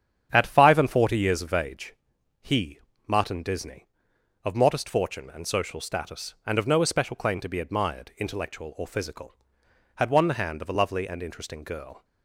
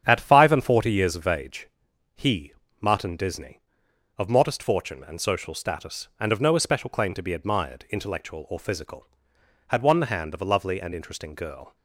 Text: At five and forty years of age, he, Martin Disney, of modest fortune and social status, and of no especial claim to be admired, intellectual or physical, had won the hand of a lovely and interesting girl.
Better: neither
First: starts louder than the rest; strong; until 1.3 s; 8.5 dB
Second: starts louder than the rest; strong; until 1.0 s; 8.5 dB

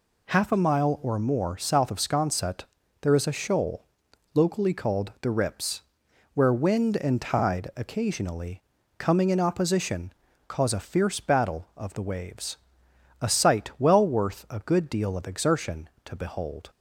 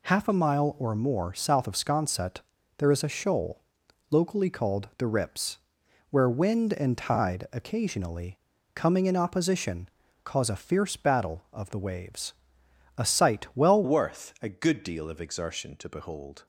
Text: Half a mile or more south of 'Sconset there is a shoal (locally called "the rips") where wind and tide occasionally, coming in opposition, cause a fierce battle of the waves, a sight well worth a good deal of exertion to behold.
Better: first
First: pauses between "Sconset" and "there"; at 2.6 s; 0.38 s long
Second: pauses between "Sconset" and "there"; at 2.3 s; 0.38 s long // changes voice at "worth"; from 13.8 s on; 2.6 s long

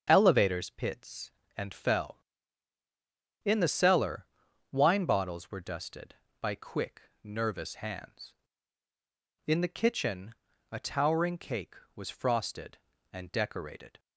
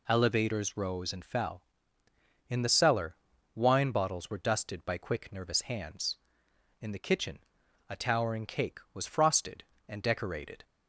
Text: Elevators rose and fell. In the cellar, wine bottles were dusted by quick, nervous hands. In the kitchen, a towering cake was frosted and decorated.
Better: second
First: starts louder than the rest; until 1.0 s; 7 dB // says "pits" for "rose"; at 0.7 s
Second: none

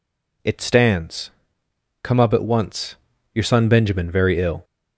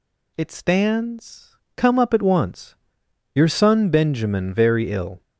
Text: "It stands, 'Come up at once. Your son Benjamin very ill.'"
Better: neither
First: none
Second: none

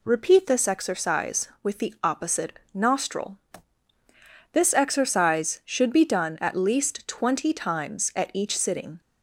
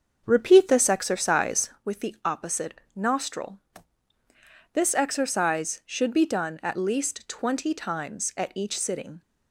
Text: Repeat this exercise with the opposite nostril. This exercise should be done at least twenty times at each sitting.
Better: first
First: none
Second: starts louder than the rest; until 1.8 s; 6.5 dB

